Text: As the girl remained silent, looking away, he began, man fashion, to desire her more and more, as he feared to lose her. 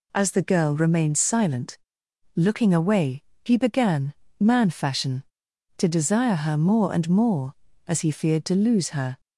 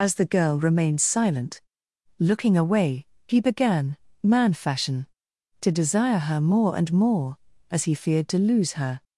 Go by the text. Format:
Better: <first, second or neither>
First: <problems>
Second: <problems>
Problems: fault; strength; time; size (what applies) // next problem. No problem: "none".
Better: first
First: none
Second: loses the start of "As"; at 0.0 s; 50 ms